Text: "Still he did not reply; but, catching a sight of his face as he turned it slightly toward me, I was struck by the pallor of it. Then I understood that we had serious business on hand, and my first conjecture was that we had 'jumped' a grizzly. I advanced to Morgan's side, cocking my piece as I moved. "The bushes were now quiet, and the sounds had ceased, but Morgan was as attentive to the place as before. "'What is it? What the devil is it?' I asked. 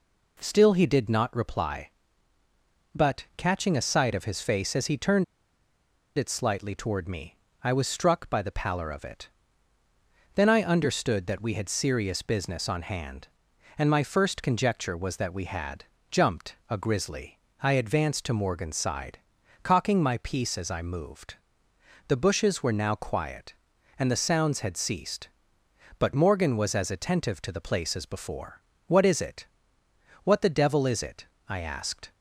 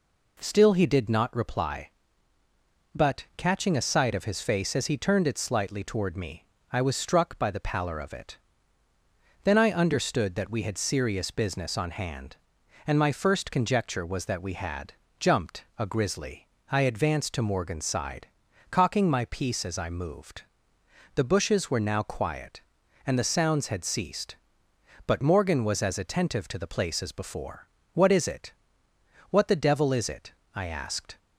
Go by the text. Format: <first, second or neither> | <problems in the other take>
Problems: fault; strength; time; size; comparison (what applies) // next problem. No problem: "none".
second | pauses between "turned" and "it"; noticeable; at 5.2 s; 0.92 s long // pauses between "had" and "jumped"; slight; at 15.8 s; 0.24 s long; slight in the second